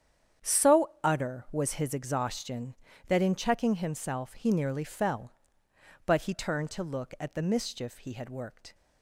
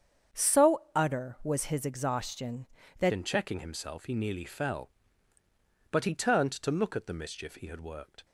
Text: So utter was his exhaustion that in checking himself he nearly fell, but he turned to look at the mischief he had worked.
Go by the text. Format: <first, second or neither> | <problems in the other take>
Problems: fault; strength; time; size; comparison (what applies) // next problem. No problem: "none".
first | starts louder than the rest; strong; until 1.5 s; 7.5 dB; strong in the first // changes voice at "in"; from 3.1 s on; 5.1 s long